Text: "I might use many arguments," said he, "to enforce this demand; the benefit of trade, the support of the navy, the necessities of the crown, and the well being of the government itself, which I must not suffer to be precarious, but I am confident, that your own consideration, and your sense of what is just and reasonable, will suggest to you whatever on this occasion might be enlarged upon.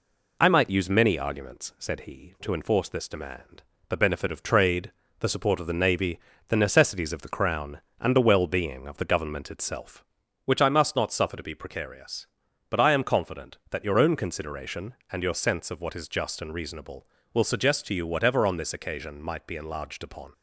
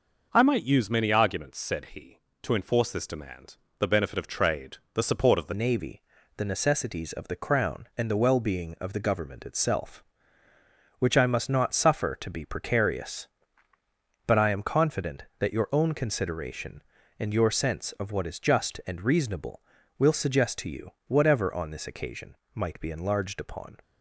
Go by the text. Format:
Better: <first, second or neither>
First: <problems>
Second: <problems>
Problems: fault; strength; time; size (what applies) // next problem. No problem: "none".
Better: first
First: none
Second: changes voice at "navy"; from 5.5 s on; 18.2 s long // pauses between "you" and "whatever"; slight; at 20.9 s; 0.16 s long // pauses between "occasion" and "might"; slight; at 22.3 s; 0.20 s long